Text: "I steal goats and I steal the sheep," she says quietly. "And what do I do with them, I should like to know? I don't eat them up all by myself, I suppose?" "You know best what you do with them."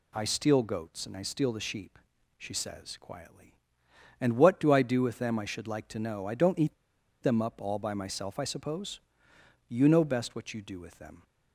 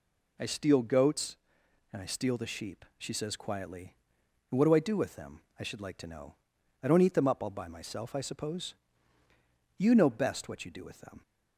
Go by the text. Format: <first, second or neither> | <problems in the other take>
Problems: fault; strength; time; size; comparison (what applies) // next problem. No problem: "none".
second | pauses between "eat" and "them"; noticeable; at 6.7 s; 0.49 s long